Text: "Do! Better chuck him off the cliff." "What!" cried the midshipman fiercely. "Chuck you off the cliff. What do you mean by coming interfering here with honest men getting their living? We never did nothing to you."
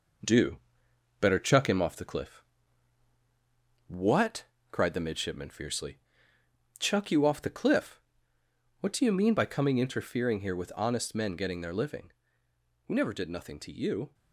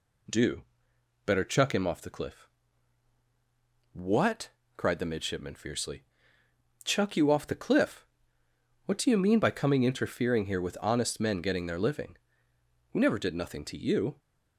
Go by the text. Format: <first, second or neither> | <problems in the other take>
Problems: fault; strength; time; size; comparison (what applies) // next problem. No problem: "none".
second | gets quieter; throughout; 3.5 dB